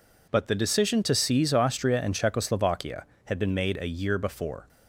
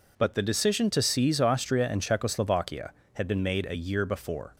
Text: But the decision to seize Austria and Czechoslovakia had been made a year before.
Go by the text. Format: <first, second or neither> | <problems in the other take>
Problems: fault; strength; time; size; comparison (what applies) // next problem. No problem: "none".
neither | none